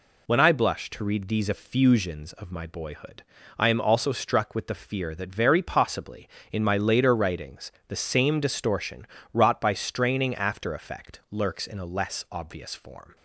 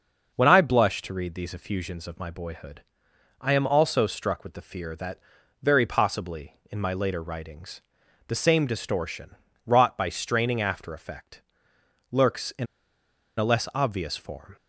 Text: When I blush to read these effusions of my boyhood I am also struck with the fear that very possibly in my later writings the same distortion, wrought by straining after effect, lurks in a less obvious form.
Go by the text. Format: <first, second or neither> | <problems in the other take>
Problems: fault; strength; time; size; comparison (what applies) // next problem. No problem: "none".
first | starts louder than the rest; noticeable; until 1.3 s; 6 dB // pauses between "boyhood" and "I"; noticeable; at 2.8 s; 0.56 s long; also in the first // pauses between "that" and "very"; at 5.1 s; 0.44 s long // pauses between "writings" and "the"; noticeable; at 7.8 s; 0.46 s long; slight in the first // pauses between "in" and "a"; noticeable; at 12.6 s; 0.71 s long